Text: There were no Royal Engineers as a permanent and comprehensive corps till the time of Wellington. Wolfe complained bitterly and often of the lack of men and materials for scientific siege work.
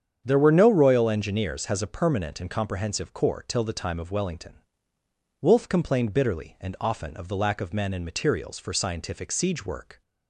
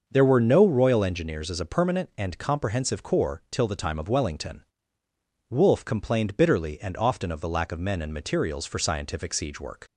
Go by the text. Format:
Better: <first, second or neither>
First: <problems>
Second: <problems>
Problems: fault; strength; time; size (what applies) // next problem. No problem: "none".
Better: second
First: starts louder than the rest; strong; until 1.2 s; 8 dB // says "has" for "as"; at 1.6 s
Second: starts louder than the rest; until 1.0 s; 6.5 dB